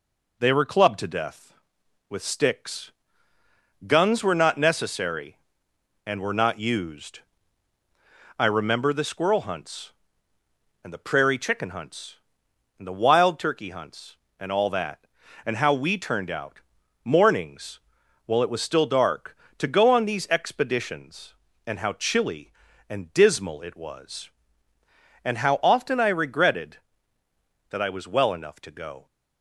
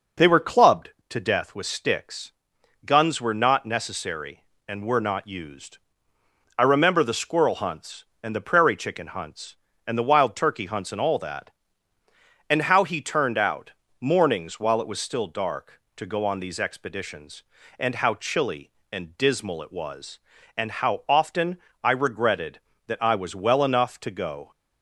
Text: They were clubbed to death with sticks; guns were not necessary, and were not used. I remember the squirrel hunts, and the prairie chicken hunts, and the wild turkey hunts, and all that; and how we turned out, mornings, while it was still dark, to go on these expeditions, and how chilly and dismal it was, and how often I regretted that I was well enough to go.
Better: first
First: none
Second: says "he" for "we"; at 12.8 s // pauses between "often" and "I"; slight; at 21.5 s; 0.22 s long

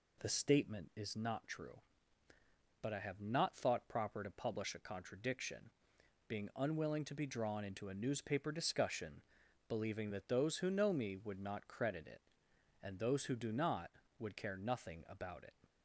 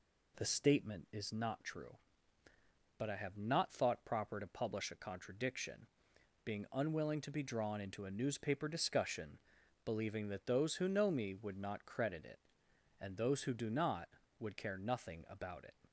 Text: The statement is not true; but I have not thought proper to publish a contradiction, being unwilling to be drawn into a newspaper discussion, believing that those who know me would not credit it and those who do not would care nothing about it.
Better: neither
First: none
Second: none

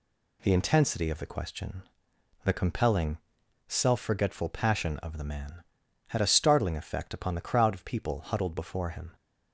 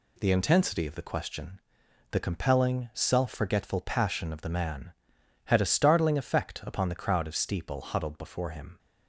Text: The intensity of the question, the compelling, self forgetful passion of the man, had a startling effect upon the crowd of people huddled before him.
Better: first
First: none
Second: says "steeple" for "people"; at 7.3 s

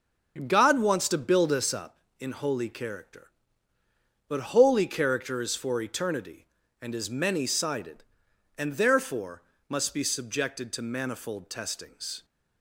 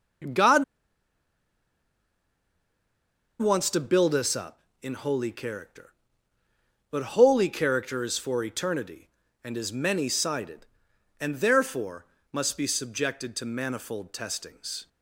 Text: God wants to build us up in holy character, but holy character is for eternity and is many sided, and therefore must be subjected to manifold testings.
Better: first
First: starts louder than the rest; until 1.4 s; 7 dB // pauses between "therefore" and "must"; slight; at 9.4 s; 0.26 s long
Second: starts louder than the rest; until 4.0 s; 7 dB // pauses between "God" and "wants"; strong; at 0.6 s; 2.7 s long // pauses between "therefore" and "must"; slight; at 12.0 s; 0.26 s long

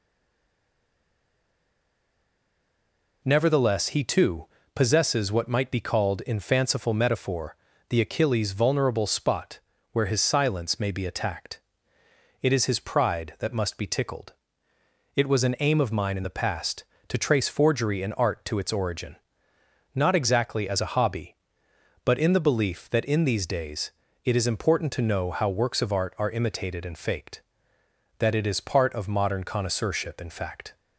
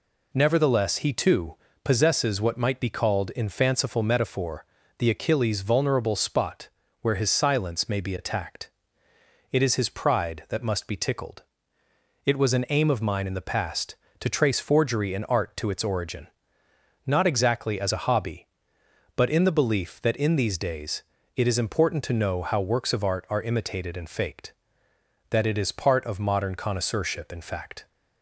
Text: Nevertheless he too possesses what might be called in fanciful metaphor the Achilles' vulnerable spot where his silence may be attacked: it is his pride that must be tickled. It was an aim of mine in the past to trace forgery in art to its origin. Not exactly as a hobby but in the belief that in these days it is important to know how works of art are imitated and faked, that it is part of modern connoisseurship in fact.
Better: second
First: stays silent before the first word; strong; until 3.2 s; 3.2 s long // pauses between "too" and "possesses"; slight; at 4.4 s; 0.28 s long // pauses between "metaphor" and "the"; slight; at 7.5 s; 0.32 s long // pauses between "spot" and "where"; slight; at 9.5 s; 0.34 s long // pauses between "days" and "it"; slight; at 23.9 s; 0.34 s long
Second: pauses between "too" and "possesses"; slight; at 1.5 s; 0.28 s long // pauses between "metaphor" and "the"; slight; at 4.6 s; 0.32 s long // pauses between "spot" and "where"; slight; at 6.6 s; 0.34 s long // pauses between "days" and "it"; slight; at 21.0 s; 0.34 s long

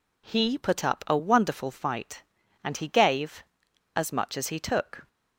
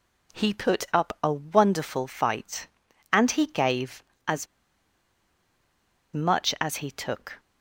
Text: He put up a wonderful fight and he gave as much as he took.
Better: first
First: none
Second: pauses between "as" and "much"; strong; at 4.4 s; 1.6 s long

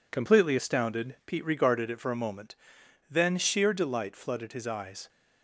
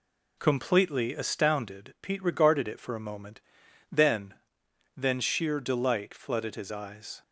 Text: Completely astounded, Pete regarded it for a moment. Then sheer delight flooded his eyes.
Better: first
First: none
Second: says "Then" twice; at 4.9 s

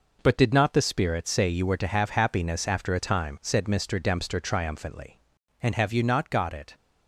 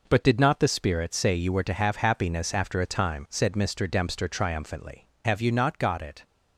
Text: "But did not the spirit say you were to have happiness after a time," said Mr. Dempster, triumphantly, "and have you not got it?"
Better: first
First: none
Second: skips "and"; at 5.1 s

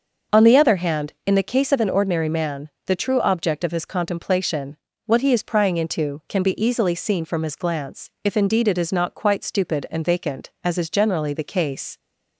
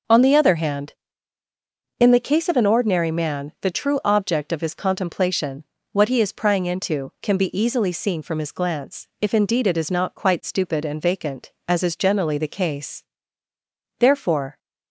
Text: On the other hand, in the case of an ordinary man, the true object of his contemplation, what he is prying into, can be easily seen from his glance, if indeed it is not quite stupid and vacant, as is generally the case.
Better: first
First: starts louder than the rest; until 1.4 s; 6.5 dB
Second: starts louder than the rest; noticeable; until 2.1 s; 6 dB // goes on to say "Therefore"; from 13.9 s on; 0.60 s long

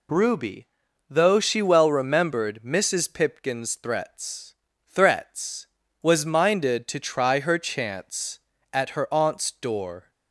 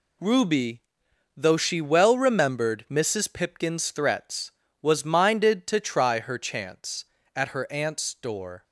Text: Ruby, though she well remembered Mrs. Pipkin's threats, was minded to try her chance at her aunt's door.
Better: second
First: says "threats" twice; at 4.9 s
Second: none

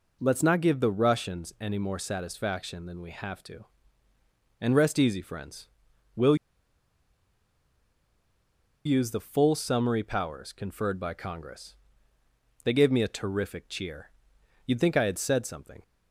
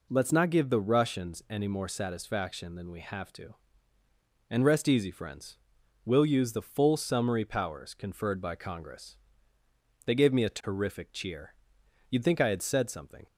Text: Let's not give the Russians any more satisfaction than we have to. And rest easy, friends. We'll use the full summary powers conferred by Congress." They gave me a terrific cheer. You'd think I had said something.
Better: second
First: pauses between "We'll" and "use"; strong; at 6.3 s; 2.5 s long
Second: none

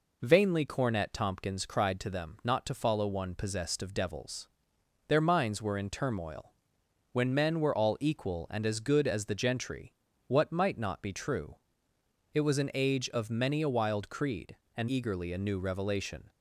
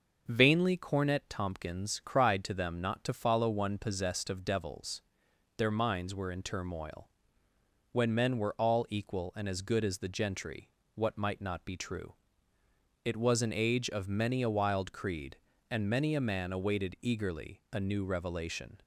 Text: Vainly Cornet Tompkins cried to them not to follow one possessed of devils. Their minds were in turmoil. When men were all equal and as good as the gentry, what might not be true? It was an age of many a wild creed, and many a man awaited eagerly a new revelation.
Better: second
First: skips "many a man awaited"; at 14.8 s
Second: none

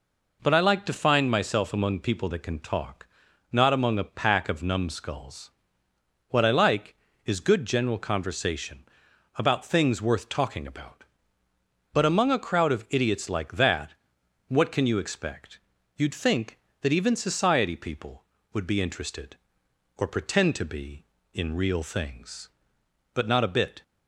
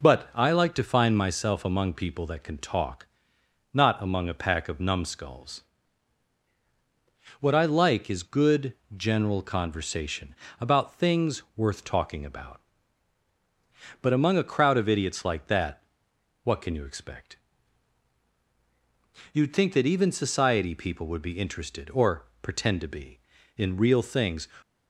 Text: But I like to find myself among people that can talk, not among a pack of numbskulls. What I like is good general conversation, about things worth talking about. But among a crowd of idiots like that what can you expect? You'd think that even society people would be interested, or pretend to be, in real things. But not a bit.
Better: first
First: pauses between "that" and "what"; noticeable; at 13.9 s; 0.54 s long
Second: pauses between "good" and "general"; slight; at 8.7 s; 0.22 s long // pauses between "that" and "what"; noticeable; at 15.7 s; 0.66 s long // pauses between "or" and "pretend"; slight; at 22.2 s; 0.16 s long // stops before "But not a bit"; at 24.6 s

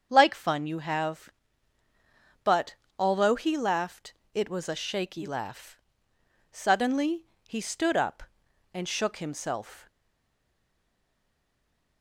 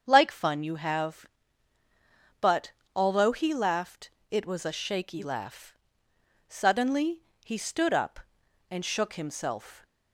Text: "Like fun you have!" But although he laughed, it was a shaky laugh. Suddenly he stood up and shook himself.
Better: second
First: starts louder than the rest; strong; until 1.1 s; 7 dB // pauses between "But" and "although"; slight; at 2.7 s; 0.24 s long // pauses between "Suddenly" and "he"; slight; at 7.2 s; 0.22 s long // stays silent after the last word; from 9.8 s on; 2.2 s long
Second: starts louder than the rest; strong; until 1.0 s; 7 dB // pauses between "But" and "although"; slight; at 2.7 s; 0.24 s long // pauses between "Suddenly" and "he"; slight; at 7.2 s; 0.22 s long

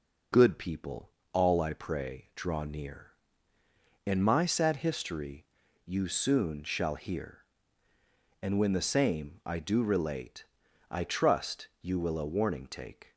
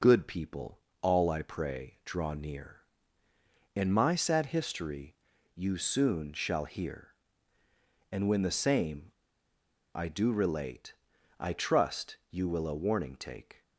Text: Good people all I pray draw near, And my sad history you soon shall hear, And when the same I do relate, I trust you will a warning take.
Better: first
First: pauses between "people" and "all"; slight; at 1.1 s; 0.20 s long // pauses between "history" and "you"; at 5.4 s; 0.40 s long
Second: pauses between "people" and "all"; slight; at 0.8 s; 0.20 s long // pauses between "history" and "you"; at 5.1 s; 0.40 s long // pauses between "same" and "I"; noticeable; at 9.1 s; 0.82 s long

